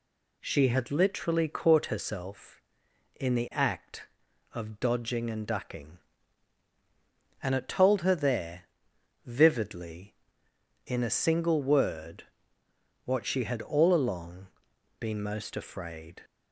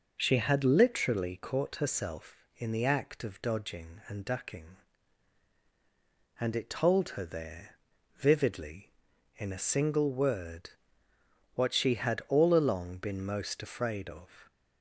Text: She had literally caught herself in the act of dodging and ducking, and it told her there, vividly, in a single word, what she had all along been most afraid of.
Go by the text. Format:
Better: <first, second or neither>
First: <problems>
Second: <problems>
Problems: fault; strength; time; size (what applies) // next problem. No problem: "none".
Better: second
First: pauses between "along" and "been"; noticeable; at 14.4 s; 0.52 s long // stops before "of"; at 16.2 s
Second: none